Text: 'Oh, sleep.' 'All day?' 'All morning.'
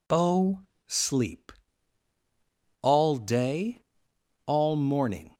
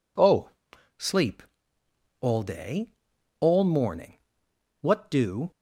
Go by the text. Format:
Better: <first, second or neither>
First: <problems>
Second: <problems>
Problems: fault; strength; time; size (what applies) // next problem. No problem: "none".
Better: first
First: none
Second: goes on to say "What do"; noticeable; from 4.8 s on; 0.70 s long